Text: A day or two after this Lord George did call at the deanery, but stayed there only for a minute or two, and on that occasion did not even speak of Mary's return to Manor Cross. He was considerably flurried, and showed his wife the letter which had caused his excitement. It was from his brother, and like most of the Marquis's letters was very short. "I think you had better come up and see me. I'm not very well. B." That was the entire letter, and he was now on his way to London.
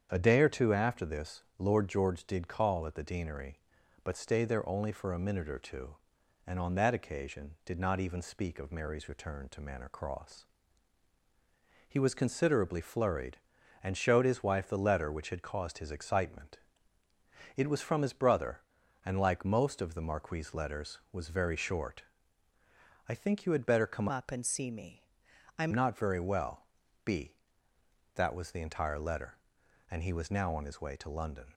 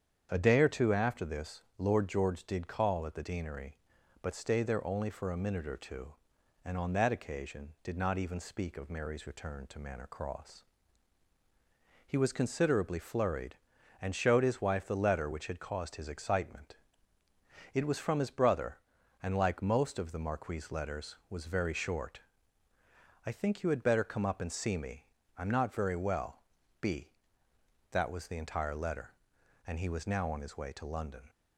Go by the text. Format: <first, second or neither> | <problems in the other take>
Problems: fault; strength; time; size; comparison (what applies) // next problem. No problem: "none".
second | starts louder than the rest; strong; until 1.1 s; 8 dB; strong in the second // changes voice from "up" to "I'm"; from 24.1 to 25.7 s; 1.6 s long